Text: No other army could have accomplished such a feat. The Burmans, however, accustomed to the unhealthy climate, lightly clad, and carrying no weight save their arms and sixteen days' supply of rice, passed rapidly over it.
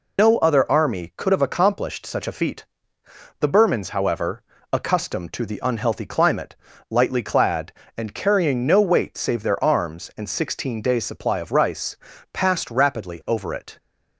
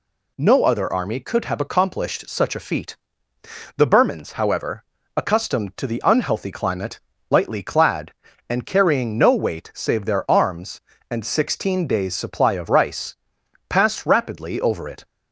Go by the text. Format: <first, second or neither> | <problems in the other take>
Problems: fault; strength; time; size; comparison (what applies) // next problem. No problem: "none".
second | loses the start of "No"; at 0.1 s; 85 ms